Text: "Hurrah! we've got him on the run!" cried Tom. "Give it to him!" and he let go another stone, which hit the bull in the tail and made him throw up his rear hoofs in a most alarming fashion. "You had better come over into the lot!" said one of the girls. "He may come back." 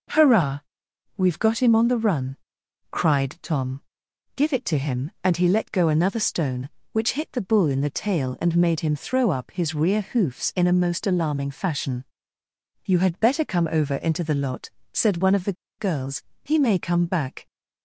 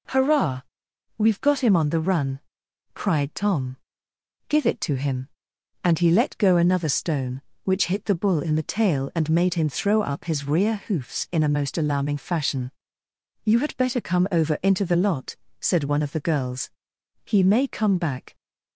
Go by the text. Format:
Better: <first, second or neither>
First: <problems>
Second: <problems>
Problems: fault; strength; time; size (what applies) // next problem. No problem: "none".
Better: second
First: pauses between "the" and "girls"; slight; at 15.5 s; 0.26 s long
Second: none